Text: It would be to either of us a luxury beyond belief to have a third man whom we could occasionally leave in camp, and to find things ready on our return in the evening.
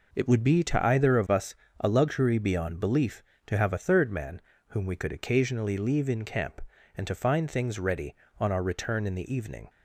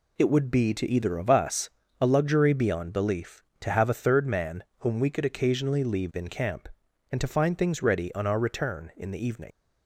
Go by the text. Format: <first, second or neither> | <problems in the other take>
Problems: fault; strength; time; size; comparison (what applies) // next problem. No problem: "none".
first | pauses between "us" and "a"; slight; at 1.6 s; 0.30 s long; slight in the first // pauses between "man" and "whom"; slight; at 4.6 s; 0.16 s long; slight in the first // leaves "evening" unfinished; at 9.5 s; 35 ms